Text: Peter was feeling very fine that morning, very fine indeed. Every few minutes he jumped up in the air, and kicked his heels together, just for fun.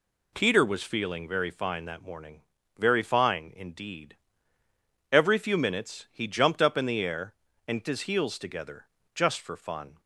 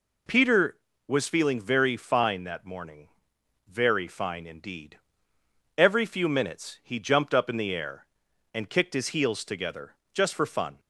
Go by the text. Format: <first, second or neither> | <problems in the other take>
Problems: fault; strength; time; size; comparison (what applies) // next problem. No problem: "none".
second | skips "kicked"; at 7.8 s